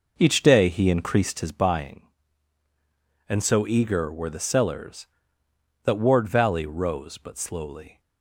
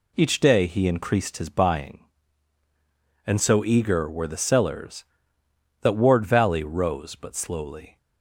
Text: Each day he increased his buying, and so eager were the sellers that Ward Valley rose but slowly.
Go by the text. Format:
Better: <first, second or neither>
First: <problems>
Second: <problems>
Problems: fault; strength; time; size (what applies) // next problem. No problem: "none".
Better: second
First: starts louder than the rest; noticeable; until 1.6 s; 5 dB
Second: none